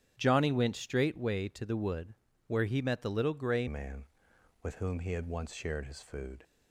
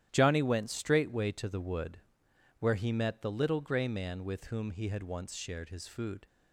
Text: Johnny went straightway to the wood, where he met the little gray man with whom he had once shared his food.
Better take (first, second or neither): second